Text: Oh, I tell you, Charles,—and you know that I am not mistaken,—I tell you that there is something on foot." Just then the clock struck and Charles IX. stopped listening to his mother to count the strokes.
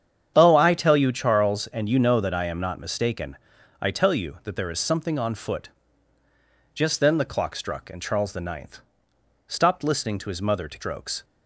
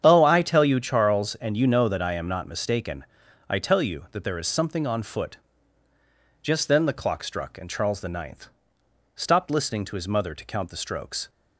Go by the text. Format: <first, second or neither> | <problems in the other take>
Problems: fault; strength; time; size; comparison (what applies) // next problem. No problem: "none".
second | starts louder than the rest; strong; until 1.3 s; 8.5 dB; strong in the second // skips "count the"; at 10.7 s